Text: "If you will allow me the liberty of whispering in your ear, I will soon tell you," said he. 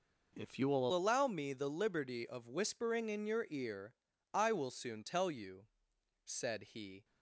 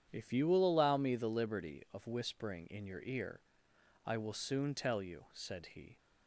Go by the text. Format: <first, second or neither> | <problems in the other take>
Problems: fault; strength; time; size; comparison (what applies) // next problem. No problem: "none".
second | changes voice at "allow"; from 0.9 s on; 6.1 s long